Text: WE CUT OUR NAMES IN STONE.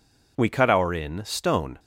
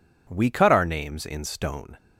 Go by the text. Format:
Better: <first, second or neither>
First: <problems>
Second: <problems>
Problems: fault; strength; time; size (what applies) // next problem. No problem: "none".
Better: second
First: skips "NAMES"; at 0.9 s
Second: none